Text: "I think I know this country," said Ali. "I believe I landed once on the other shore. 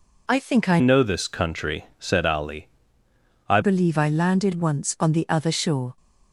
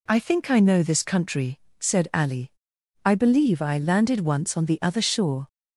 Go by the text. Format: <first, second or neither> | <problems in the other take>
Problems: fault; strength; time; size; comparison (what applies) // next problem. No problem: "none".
second | changes voice from "know" to "I"; from 0.7 to 3.5 s; 2.8 s long